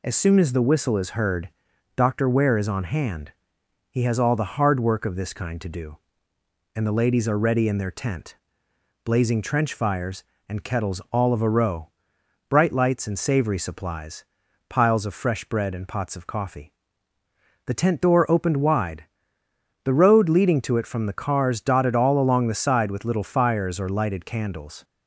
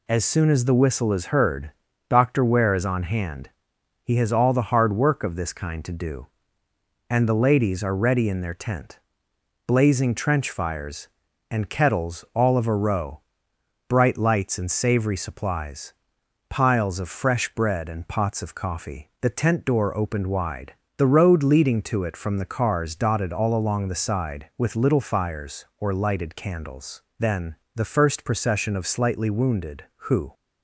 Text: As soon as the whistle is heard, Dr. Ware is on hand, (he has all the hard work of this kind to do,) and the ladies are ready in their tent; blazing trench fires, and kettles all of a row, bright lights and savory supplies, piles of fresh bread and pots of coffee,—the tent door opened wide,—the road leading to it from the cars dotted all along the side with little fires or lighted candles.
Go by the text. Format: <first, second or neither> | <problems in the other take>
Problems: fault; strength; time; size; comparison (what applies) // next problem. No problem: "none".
first | goes on to say "Then the first procession of slightly wounded who"; strong; from 27.1 s on; 3.1 s long